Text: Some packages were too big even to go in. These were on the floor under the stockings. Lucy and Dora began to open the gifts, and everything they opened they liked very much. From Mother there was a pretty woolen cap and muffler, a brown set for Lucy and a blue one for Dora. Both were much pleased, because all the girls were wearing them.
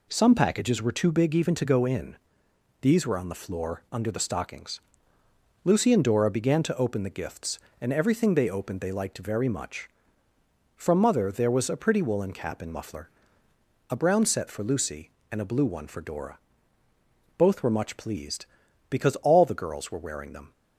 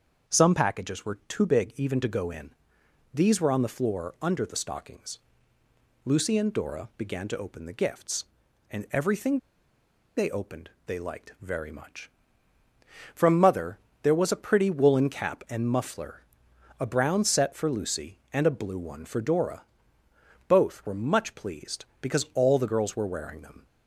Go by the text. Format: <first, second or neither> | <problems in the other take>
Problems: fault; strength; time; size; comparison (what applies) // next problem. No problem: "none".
first | starts louder than the rest; until 1.3 s; 7 dB // pauses between "everything" and "they"; noticeable; at 9.3 s; 0.78 s long // pauses between "opened" and "they"; slight; at 10.6 s; 0.16 s long // pauses between "Mother" and "there"; slight; at 13.7 s; 0.24 s long